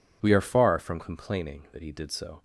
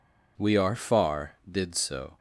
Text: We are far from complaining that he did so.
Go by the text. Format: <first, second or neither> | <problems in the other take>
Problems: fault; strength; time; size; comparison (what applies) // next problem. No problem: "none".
first | skips "from complaining that he"; at 1.4 s